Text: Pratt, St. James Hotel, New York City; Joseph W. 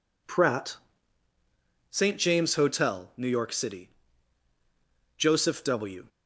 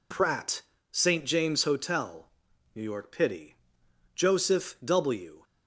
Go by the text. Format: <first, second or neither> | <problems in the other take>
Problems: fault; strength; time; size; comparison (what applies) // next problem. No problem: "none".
first | says "Pity" for "City"; at 3.1 s